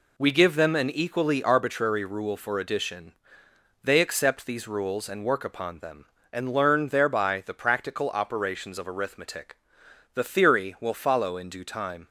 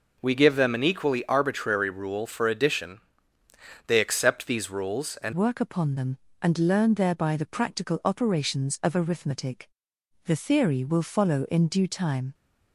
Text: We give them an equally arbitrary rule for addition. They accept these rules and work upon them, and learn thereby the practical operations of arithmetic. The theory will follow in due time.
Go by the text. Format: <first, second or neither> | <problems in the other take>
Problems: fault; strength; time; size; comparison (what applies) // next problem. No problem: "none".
first | changes voice at "work"; from 5.3 s on; 7.0 s long